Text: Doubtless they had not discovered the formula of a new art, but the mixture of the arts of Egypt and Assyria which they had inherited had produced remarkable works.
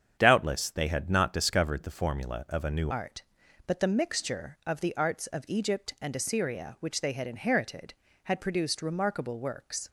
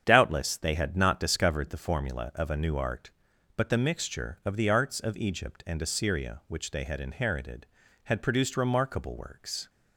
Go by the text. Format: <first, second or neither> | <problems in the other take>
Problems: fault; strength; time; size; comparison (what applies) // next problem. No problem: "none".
second | starts louder than the rest; strong; until 1.2 s; 8 dB; strong in the second // changes voice at "art"; from 2.9 s on; 6.9 s long